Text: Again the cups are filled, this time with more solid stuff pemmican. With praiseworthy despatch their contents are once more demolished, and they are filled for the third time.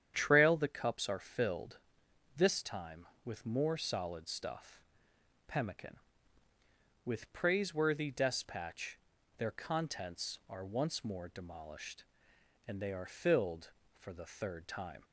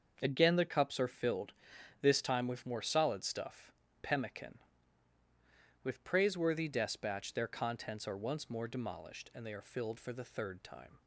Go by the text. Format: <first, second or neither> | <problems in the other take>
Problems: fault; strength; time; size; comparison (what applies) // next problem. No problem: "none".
second | starts louder than the rest; strong; until 1.1 s; 9 dB; also in the second // says "Trail" for "Again"; at 0.1 s // pauses between "stuff" and "pemmican"; noticeable; at 4.8 s; 0.68 s long; slight in the second // pauses between "despatch" and "their"; at 8.9 s; 0.42 s long